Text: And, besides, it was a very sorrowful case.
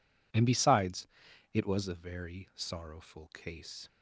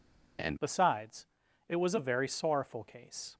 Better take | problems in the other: first | changes voice at "besides"; from 0.5 s on; 2.8 s long

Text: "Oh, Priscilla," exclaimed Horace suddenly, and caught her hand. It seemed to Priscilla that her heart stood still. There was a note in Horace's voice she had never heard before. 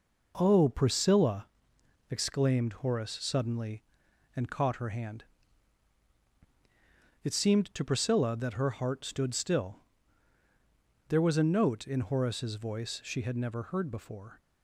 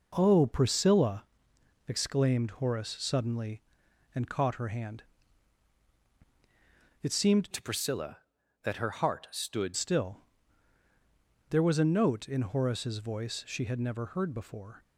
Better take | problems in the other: first | changes voice from "to" to "stood"; from 7.5 to 9.7 s; 2.2 s long

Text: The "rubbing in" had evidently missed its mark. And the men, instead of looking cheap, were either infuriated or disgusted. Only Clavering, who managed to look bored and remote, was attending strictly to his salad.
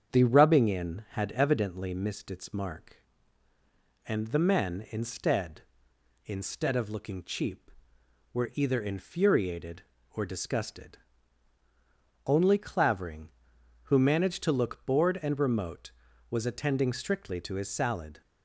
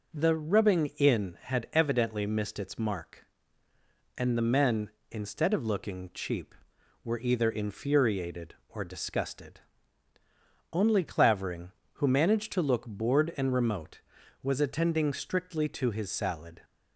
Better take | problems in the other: second | starts louder than the rest; strong; until 1.1 s; 7.5 dB // says "instead" twice; at 6.2 s

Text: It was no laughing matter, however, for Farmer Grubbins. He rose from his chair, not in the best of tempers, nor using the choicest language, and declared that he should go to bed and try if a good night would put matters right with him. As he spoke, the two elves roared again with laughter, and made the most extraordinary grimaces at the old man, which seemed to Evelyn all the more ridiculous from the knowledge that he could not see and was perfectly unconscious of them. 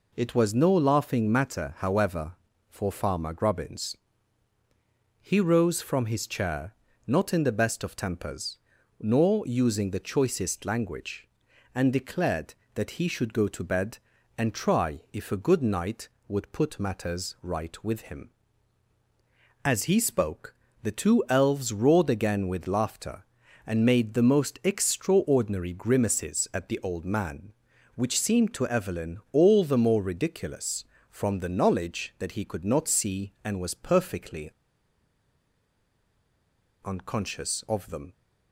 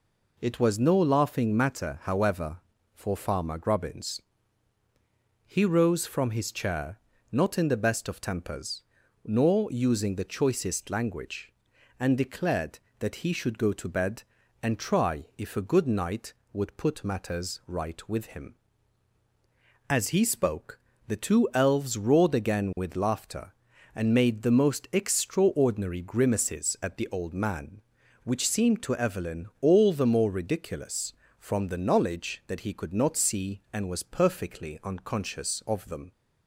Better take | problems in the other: second | pauses between "perfectly" and "unconscious"; strong; at 34.5 s; 2.3 s long

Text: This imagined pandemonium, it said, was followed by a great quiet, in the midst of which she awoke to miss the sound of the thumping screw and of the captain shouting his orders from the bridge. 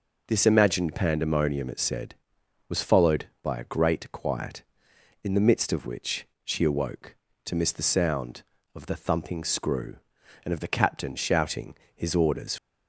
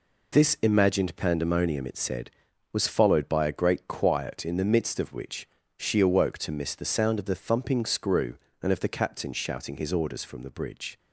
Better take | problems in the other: second | pauses between "which" and "she"; slight; at 6.2 s; 0.20 s long; slight in the second // pauses between "shouting" and "his"; slight; at 11.7 s; 0.18 s long // stops before "from the bridge"; at 12.5 s

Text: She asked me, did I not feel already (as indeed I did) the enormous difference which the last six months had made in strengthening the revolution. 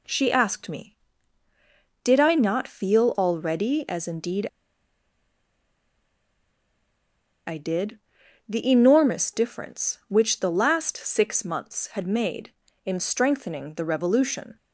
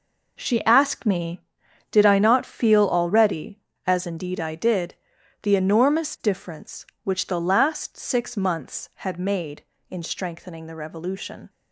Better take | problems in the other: second | pauses between "indeed" and "I"; strong; at 4.4 s; 3.0 s long

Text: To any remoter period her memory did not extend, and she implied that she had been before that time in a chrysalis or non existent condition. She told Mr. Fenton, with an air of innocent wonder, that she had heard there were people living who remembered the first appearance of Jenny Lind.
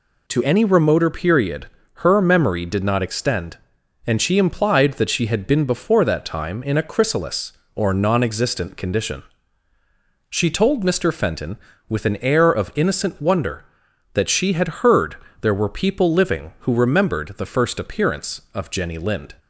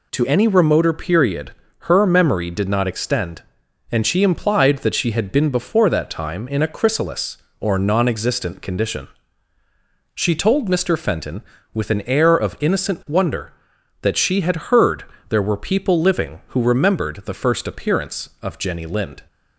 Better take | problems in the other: neither | pauses between "period" and "her"; slight; the same in both // pauses between "heard" and "there"; slight; the same in both

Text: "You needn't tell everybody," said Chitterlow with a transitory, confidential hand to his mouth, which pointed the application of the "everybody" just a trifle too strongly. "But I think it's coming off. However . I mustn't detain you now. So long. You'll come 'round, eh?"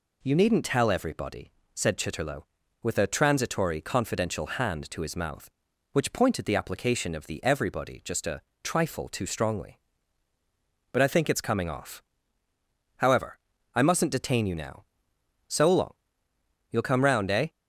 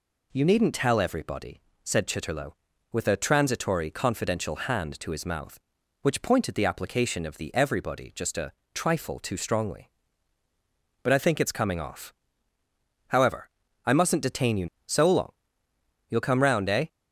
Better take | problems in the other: first | pauses between "a" and "trifle"; slight; at 8.5 s; 0.22 s long; slight in the first // skips "now"; at 14.7 s

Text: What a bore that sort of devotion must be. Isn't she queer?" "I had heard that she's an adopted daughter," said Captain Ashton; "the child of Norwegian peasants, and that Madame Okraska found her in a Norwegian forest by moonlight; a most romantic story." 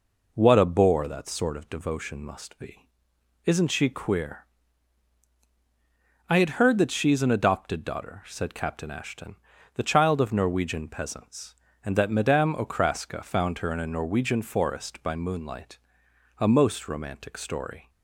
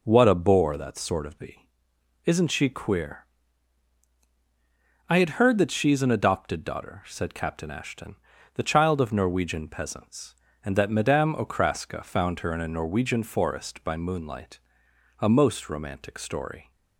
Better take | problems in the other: first | skips "devotion must"; at 1.3 s

